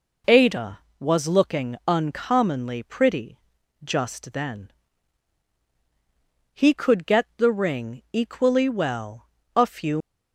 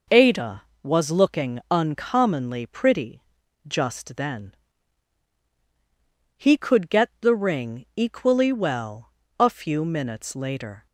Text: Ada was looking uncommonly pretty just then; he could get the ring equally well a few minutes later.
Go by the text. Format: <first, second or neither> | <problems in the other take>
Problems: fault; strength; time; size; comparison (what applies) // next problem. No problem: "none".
second | pauses between "pretty" and "just"; noticeable; at 3.3 s; 0.46 s long; noticeable in the second // pauses between "well" and "a"; slight; at 9.2 s; 0.26 s long; slight in the second // stops before "minutes later"; at 10.0 s